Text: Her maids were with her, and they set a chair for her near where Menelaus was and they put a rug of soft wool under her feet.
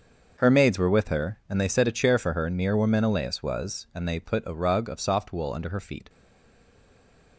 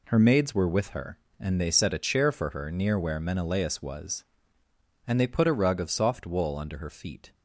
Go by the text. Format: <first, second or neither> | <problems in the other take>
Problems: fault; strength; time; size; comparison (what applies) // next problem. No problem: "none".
second | starts louder than the rest; until 1.3 s; 6.5 dB // stays silent after the last word; noticeable; from 6.0 s on; 1.3 s long